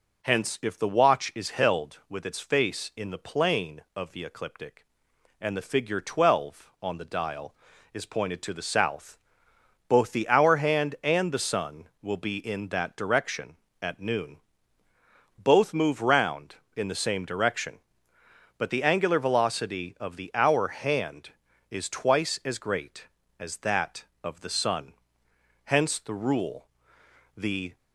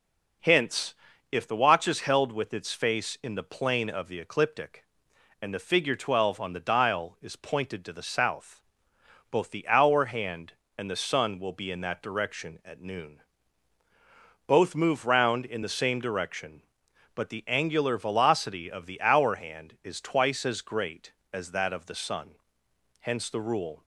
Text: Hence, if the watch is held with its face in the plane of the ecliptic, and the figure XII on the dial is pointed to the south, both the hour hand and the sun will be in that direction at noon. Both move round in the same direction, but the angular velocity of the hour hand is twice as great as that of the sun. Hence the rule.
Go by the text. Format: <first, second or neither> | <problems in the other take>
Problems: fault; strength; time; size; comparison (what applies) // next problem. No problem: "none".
second | goes on to say "The"; slight; from 27.3 s on; 0.40 s long